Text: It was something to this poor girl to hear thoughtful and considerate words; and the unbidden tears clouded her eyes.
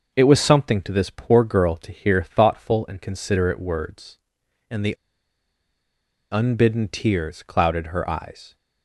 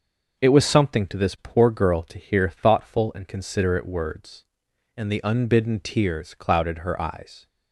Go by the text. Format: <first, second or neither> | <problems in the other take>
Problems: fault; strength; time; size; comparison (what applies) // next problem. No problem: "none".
second | pauses between "the" and "unbidden"; strong; at 4.9 s; 1.3 s long